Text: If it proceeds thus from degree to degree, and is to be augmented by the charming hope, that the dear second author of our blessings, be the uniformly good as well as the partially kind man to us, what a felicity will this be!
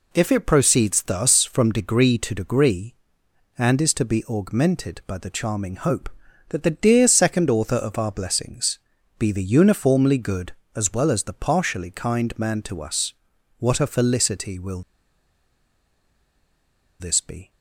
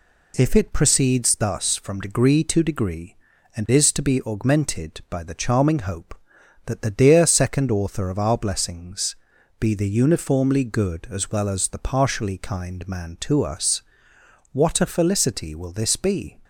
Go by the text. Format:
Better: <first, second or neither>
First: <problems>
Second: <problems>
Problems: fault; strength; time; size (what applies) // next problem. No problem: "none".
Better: second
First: pauses between "will" and "this"; strong; at 14.8 s; 2.1 s long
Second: none